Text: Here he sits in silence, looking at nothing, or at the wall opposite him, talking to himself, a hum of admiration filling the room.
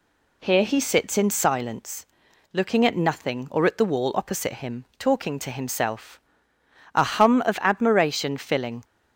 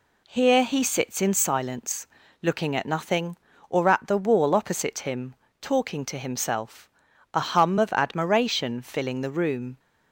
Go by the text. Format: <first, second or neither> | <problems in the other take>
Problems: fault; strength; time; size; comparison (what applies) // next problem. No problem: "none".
second | stops before "the room"; at 8.8 s